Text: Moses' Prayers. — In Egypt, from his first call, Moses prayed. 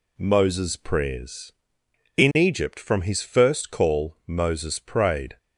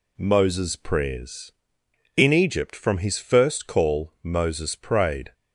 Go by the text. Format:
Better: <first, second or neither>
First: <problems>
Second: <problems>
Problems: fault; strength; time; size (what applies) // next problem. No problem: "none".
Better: neither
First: none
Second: none